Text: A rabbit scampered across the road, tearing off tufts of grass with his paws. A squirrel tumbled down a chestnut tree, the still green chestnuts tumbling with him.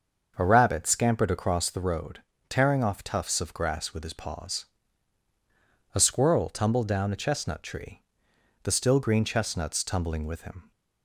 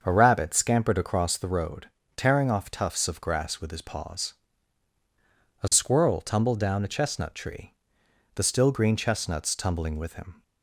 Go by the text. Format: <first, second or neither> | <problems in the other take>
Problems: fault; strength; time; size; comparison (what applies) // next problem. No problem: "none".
neither | starts louder than the rest; the same in both